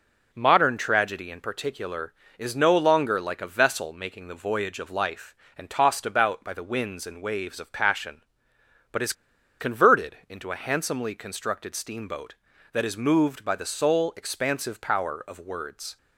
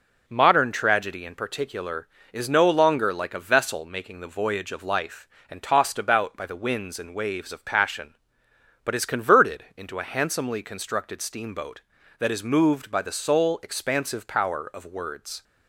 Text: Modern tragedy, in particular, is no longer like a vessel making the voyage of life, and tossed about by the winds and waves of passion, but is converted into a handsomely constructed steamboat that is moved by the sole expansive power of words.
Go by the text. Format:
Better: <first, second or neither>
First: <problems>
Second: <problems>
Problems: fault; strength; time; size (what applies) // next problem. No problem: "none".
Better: second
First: pauses between "is" and "converted"; noticeable; at 9.1 s; 0.47 s long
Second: none